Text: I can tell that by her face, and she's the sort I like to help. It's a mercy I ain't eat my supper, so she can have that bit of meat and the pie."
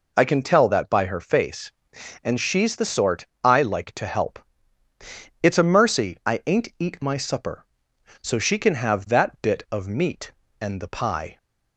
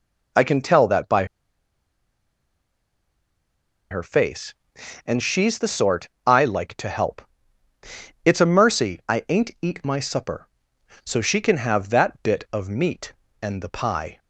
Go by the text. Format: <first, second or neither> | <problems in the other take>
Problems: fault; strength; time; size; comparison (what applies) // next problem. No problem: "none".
first | pauses between "by" and "her"; strong; at 1.2 s; 2.6 s long // pauses between "sort" and "I"; slight; at 6.0 s; 0.16 s long; slight in the first